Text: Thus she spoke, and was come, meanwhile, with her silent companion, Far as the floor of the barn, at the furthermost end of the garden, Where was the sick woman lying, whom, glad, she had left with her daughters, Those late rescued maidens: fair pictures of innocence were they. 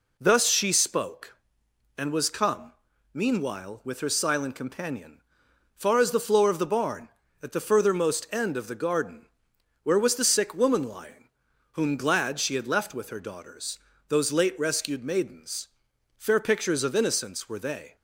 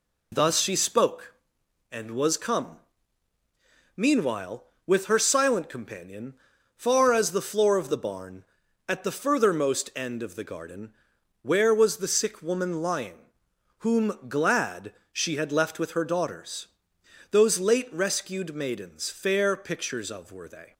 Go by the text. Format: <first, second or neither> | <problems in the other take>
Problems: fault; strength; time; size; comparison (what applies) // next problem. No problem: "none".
first | skips "innocence"; at 20.3 s